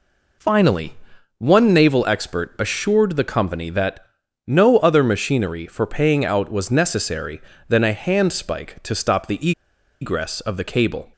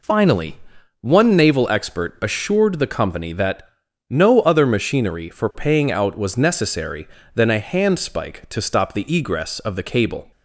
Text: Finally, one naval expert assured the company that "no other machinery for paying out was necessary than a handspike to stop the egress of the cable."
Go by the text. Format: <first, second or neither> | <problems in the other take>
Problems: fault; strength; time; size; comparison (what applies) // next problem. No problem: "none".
second | pauses between "that" and "no"; at 4.0 s; 0.42 s long; also in the second // pauses between "the" and "egress"; noticeable; at 9.5 s; 0.50 s long